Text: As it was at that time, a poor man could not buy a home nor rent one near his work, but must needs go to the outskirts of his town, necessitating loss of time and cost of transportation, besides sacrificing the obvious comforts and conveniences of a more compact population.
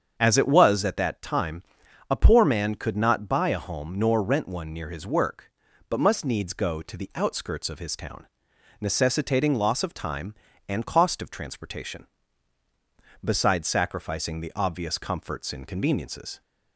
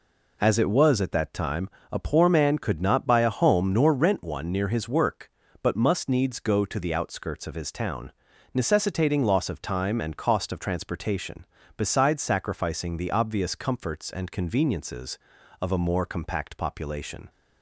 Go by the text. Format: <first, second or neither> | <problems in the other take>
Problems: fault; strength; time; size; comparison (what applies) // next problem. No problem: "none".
second | starts louder than the rest; strong; until 1.1 s; 7.5 dB // stops before "of a more compact population"; at 16.4 s